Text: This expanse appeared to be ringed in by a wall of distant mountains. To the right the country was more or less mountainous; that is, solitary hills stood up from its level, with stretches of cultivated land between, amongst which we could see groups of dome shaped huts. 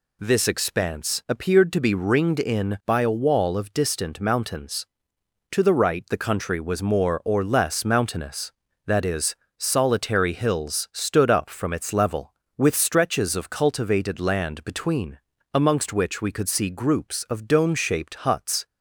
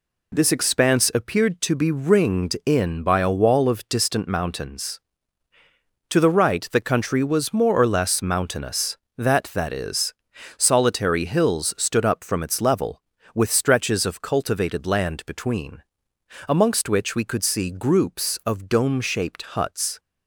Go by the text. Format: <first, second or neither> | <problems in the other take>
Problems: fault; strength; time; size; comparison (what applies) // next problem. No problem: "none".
first | says "that" twice; at 9.5 s